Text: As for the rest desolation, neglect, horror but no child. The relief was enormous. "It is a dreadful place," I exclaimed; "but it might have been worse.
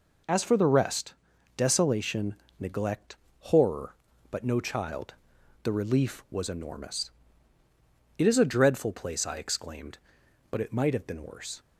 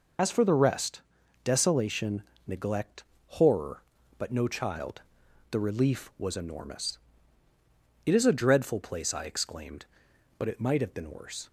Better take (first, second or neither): first